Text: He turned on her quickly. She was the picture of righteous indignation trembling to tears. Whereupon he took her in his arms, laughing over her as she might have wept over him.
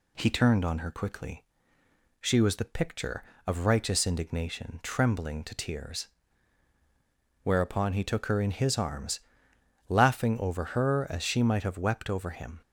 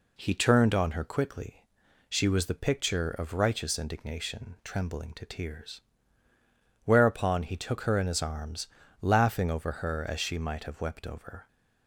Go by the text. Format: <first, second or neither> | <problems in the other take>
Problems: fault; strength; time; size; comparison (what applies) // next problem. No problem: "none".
first | stops before "him"; at 11.4 s